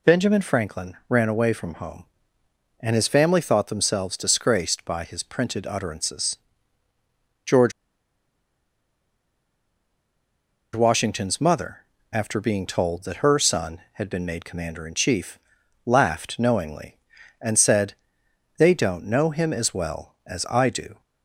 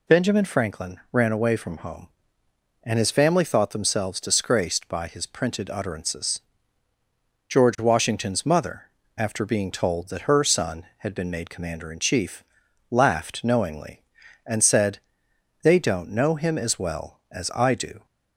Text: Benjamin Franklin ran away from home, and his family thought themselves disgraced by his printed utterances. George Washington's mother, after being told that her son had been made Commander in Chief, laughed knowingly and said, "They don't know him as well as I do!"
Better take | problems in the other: second | pauses between "George" and "Washington's"; strong; at 7.7 s; 3.0 s long

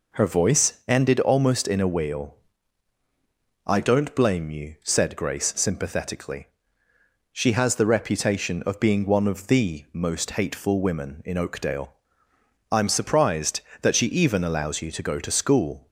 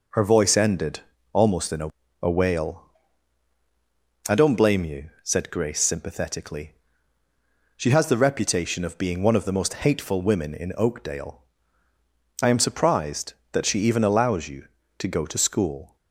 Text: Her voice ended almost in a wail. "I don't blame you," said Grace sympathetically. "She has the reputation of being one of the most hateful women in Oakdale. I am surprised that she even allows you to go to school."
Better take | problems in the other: first | pauses between "ended" and "almost"; slight; at 1.0 s; 0.32 s long // says "a" twice; at 2.2 s

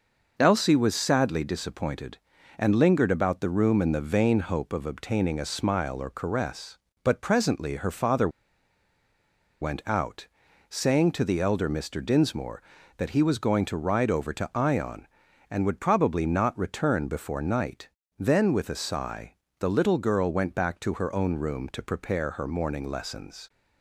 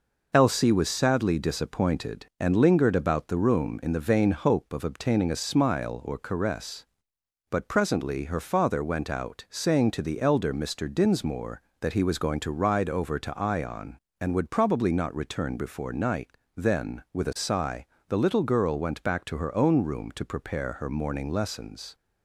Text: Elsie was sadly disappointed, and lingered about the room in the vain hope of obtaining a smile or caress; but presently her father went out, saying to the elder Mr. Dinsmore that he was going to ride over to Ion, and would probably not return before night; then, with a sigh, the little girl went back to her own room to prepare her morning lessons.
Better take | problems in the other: second | pauses between "father" and "went"; strong; at 8.2 s; 1.3 s long

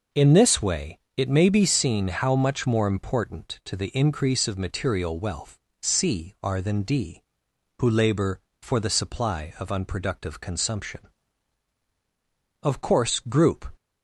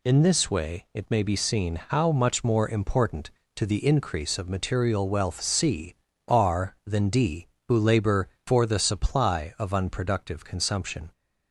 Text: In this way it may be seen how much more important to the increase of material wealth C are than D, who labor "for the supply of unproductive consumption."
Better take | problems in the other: second | pauses between "way" and "it"; slight; at 0.9 s; 0.18 s long // pauses between "wealth" and "C"; slight; at 5.5 s; 0.24 s long // goes on to say "Of course group"; noticeable; from 12.6 s on; 1.1 s long

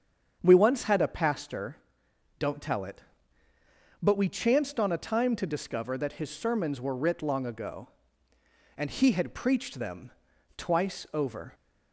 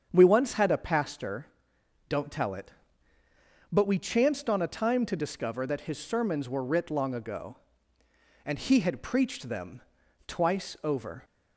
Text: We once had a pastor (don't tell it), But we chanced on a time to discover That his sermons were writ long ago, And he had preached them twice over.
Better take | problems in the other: neither | starts louder than the rest; strong; the same in both // pauses between "them" and "twice"; noticeable; the same in both

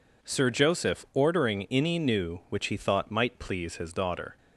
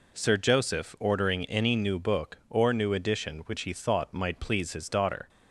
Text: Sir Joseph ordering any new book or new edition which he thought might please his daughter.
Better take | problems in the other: second | skips "book or new edition"; at 2.4 s

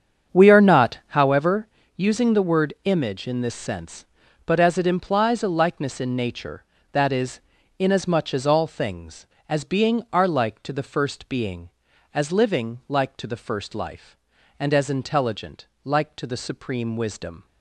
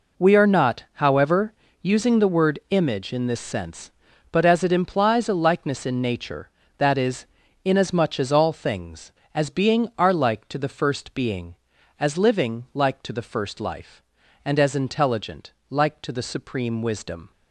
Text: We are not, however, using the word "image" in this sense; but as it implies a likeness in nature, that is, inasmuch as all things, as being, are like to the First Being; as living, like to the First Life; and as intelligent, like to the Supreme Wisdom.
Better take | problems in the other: second | starts louder than the rest; strong; until 1.3 s; 7.5 dB

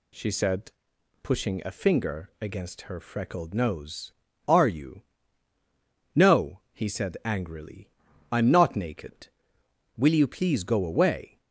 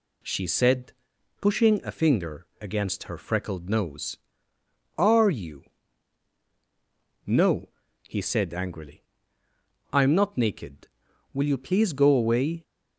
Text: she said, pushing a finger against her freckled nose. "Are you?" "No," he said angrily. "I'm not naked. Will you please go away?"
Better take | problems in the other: neither | none

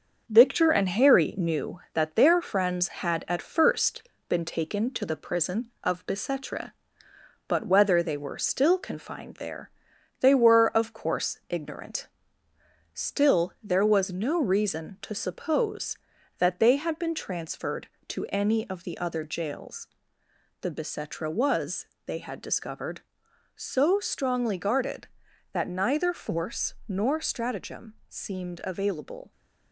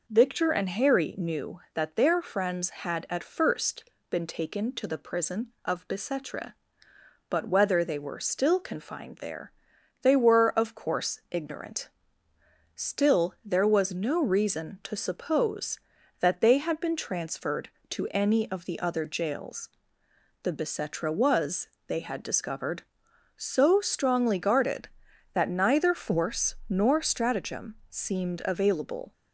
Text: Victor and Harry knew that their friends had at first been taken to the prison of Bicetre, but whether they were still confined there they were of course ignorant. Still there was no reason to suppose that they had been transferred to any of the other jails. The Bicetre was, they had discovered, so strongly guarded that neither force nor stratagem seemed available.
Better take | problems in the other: second | gets quieter; noticeable; throughout; 4.5 dB // pauses between "first" and "been"; slight; at 4.0 s; 0.26 s long; slight in the second // pauses between "there" and "they"; noticeable; at 9.6 s; 0.52 s long; noticeable in the second // pauses between "stratagem" and "seemed"; slight; at 27.9 s; 0.16 s long; slight in the second

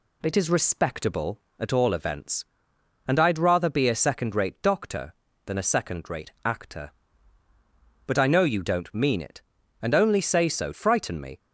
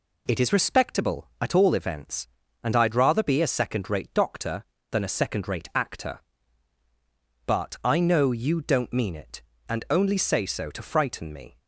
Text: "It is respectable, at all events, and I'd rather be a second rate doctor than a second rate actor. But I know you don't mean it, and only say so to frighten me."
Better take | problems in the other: second | skips "to"; at 10.7 s

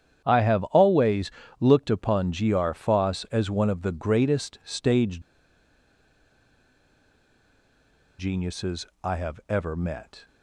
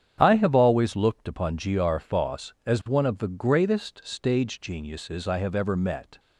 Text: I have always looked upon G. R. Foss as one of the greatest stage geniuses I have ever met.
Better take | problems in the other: second | starts louder than the rest; strong; until 1.2 s; 9 dB; strong in the second // pauses between "always" and "looked"; slight; at 1.3 s; 0.26 s long // pauses between "stage" and "geniuses"; strong; at 5.2 s; 2.9 s long // pauses between "geniuses" and "I"; slight; at 8.8 s; 0.18 s long

